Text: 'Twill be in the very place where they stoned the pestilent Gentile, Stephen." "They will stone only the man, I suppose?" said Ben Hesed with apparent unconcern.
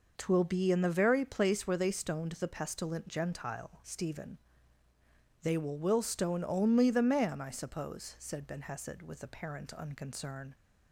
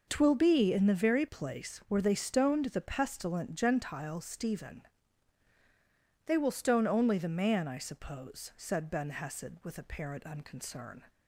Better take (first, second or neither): second